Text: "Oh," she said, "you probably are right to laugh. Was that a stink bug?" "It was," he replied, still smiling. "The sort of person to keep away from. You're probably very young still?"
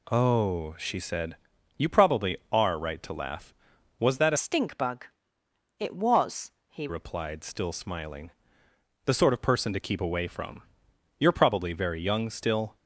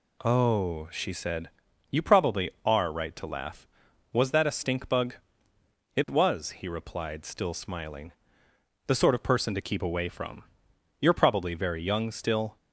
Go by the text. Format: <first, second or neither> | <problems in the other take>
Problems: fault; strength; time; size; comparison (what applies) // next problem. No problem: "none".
second | changes voice from "stink" to "he"; from 4.3 to 6.8 s; 2.5 s long